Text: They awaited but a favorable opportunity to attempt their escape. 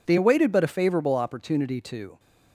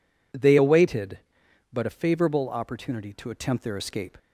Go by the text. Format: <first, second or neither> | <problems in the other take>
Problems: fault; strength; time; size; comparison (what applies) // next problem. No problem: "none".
second | stops before "attempt their escape"; at 2.1 s